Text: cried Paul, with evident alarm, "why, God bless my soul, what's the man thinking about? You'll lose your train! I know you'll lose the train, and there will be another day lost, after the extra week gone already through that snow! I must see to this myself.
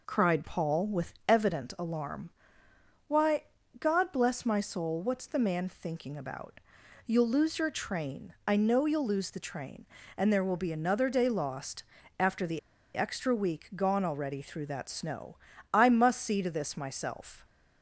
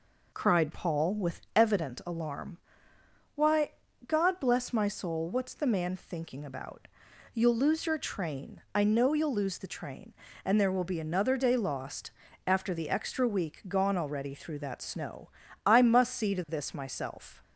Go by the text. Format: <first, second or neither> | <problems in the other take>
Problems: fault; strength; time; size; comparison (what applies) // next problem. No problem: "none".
second | pauses between "the" and "extra"; at 12.5 s; 0.36 s long